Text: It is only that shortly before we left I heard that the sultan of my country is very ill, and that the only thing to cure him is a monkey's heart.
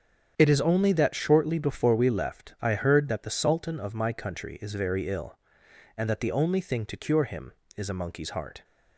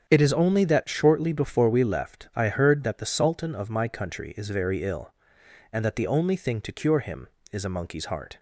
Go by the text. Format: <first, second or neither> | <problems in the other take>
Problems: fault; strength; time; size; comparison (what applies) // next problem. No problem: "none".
neither | starts louder than the rest; strong; the same in both